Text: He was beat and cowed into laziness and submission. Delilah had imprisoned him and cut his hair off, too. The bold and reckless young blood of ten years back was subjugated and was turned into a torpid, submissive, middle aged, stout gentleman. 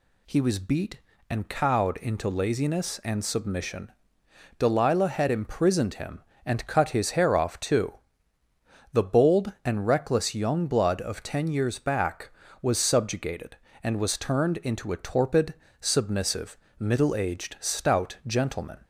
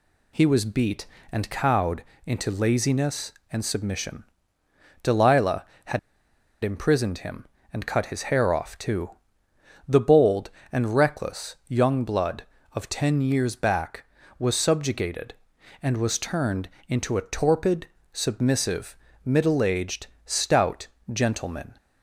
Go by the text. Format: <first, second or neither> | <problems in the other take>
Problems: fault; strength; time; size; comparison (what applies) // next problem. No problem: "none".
first | pauses between "cowed" and "into"; slight; at 2.0 s; 0.24 s long // pauses between "had" and "imprisoned"; noticeable; at 5.9 s; 0.64 s long // pauses between "turned" and "into"; slight; at 16.7 s; 0.18 s long // pauses between "stout" and "gentleman"; slight; at 20.8 s; 0.26 s long